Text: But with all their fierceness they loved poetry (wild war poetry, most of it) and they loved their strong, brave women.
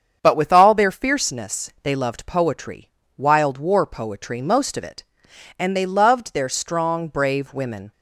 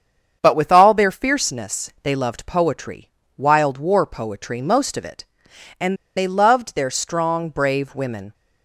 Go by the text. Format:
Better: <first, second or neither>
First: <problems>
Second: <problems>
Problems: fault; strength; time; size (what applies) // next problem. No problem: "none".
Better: first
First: starts louder than the rest; strong; until 1.2 s; 7.5 dB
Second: starts louder than the rest; strong; until 1.4 s; 7.5 dB // pauses between "and" and "they"; slight; at 5.9 s; 0.20 s long